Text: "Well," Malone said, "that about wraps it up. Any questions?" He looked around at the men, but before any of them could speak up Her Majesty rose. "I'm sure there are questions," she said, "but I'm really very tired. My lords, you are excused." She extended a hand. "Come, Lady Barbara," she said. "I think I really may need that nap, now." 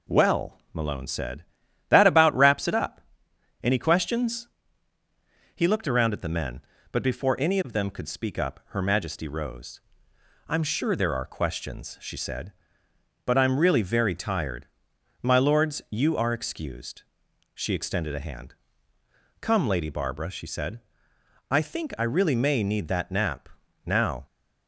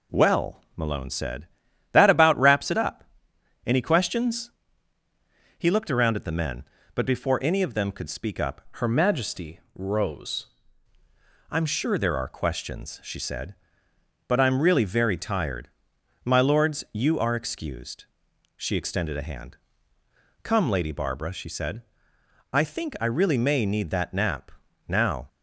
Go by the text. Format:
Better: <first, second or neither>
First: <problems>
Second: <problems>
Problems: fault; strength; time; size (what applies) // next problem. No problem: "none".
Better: first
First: none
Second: changes voice from "Her" to "rose"; from 8.7 to 10.4 s; 1.7 s long